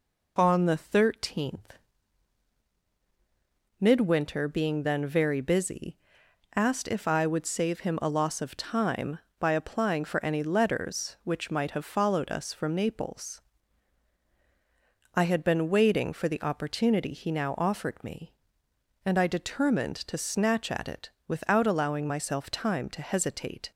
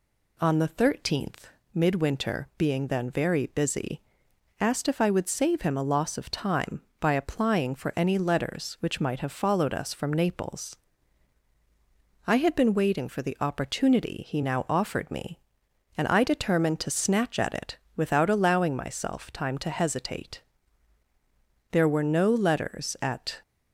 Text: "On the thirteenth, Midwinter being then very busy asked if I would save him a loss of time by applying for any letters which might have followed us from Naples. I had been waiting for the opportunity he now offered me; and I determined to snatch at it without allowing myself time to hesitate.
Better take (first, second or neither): first